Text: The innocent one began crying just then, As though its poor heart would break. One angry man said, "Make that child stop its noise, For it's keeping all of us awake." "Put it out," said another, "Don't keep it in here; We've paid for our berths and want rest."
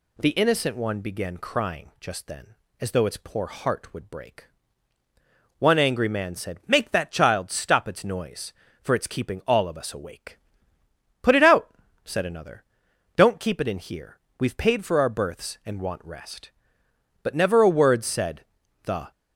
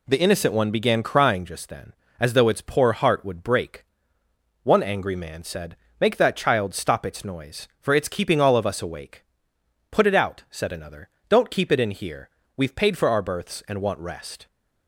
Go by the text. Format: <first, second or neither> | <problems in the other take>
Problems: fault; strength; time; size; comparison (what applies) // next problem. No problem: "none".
second | goes on to say "But never a word said the"; strong; from 17.2 s on; 1.8 s long